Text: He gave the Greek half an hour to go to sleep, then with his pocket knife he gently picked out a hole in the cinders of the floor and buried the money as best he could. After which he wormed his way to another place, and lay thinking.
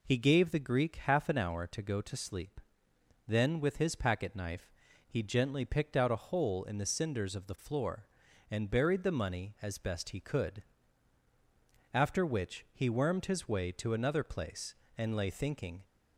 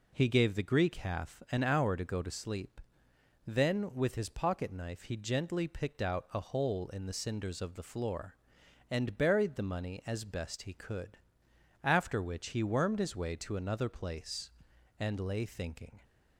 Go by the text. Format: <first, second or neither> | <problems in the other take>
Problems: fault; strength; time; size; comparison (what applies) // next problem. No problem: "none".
second | says "packet" for "pocket"; at 3.9 s // pauses between "knife" and "he"; at 4.6 s; 0.38 s long